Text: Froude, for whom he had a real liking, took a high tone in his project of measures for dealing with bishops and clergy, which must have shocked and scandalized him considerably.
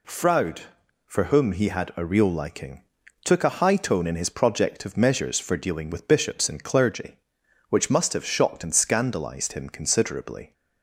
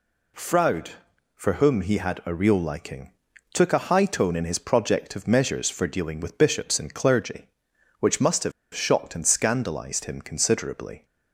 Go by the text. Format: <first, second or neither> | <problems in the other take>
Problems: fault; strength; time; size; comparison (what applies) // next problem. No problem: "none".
first | pauses between "have" and "shocked"; slight; at 8.5 s; 0.23 s long